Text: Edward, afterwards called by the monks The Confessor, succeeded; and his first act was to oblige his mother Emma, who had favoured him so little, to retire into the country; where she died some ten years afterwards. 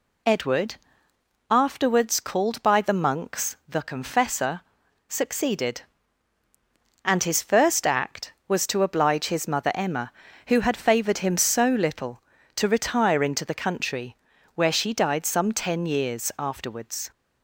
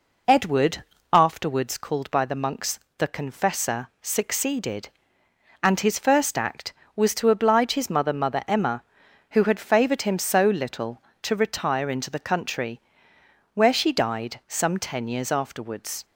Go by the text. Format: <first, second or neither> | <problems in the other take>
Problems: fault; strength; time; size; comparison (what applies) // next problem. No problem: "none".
first | pauses between "monks" and "The"; slight; at 2.7 s; 0.18 s long // says "mother" twice; at 8.1 s